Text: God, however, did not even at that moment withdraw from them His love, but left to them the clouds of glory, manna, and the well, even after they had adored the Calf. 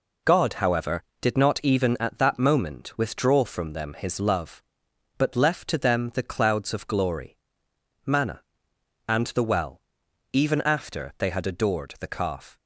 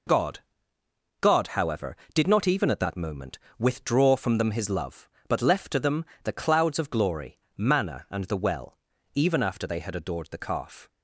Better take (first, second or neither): first